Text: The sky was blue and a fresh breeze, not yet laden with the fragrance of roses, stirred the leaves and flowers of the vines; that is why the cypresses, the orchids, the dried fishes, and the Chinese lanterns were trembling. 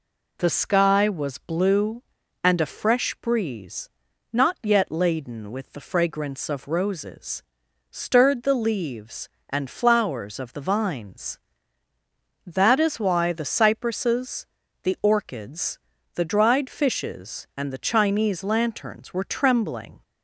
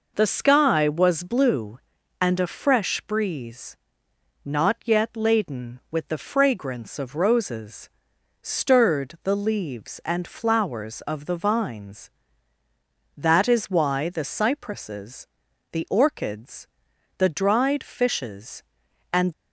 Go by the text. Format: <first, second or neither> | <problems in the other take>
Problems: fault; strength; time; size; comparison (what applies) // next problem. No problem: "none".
first | stops before "the Chinese lanterns were trembling"; at 19.3 s